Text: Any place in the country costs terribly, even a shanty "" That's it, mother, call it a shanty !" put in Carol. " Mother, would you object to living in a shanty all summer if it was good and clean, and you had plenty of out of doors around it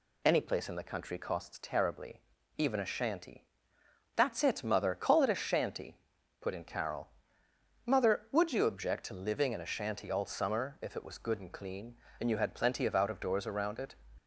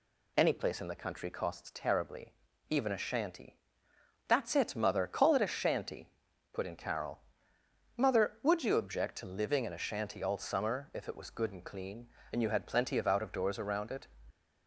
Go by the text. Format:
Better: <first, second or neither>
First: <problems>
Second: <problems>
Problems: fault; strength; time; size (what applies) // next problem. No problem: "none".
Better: neither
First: none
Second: none